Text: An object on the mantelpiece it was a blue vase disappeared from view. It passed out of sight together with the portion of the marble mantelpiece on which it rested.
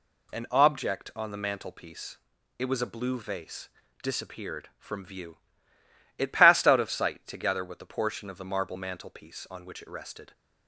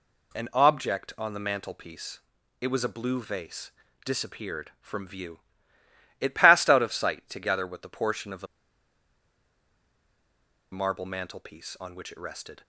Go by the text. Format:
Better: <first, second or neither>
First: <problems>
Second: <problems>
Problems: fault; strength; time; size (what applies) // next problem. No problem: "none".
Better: first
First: pauses between "mantelpiece" and "it"; at 2.1 s; 0.42 s long // pauses between "vase" and "disappeared"; slight; at 3.6 s; 0.34 s long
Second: pauses between "mantelpiece" and "it"; at 2.1 s; 0.42 s long // pauses between "vase" and "disappeared"; slight; at 3.7 s; 0.34 s long // pauses between "the" and "marble"; strong; at 8.4 s; 2.2 s long